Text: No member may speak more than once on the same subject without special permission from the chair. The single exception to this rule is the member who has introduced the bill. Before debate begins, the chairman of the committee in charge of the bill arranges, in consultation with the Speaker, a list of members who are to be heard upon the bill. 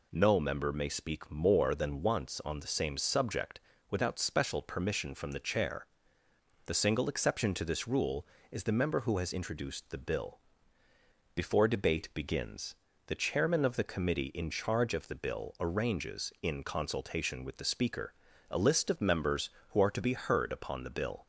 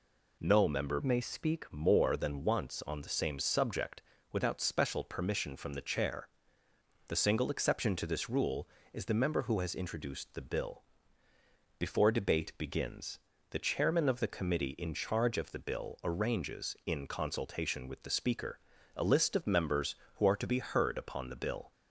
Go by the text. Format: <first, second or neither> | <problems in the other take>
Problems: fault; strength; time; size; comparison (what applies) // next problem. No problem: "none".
first | changes voice from "may" to "speak"; from 1.0 to 1.6 s; 0.6 s long // pauses between "subject" and "without"; slight; at 4.0 s; 0.30 s long; slight in the first